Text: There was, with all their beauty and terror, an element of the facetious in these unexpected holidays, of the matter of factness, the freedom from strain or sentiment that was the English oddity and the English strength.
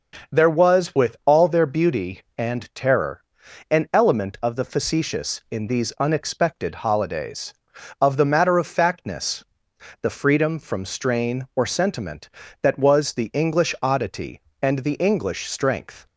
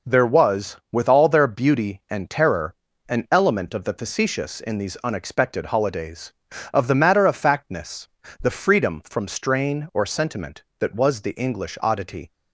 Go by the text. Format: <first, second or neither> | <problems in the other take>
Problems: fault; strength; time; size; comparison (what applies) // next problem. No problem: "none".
first | stops before "and the English strength"; at 12.3 s